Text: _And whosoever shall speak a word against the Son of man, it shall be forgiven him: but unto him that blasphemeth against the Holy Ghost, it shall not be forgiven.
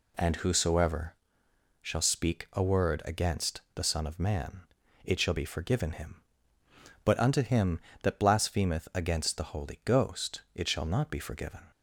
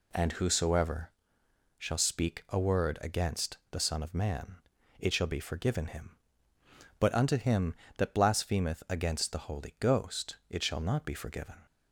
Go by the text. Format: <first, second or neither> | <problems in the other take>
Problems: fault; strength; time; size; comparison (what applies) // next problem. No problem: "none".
neither | pauses between "whosoever" and "shall"; noticeable; the same in both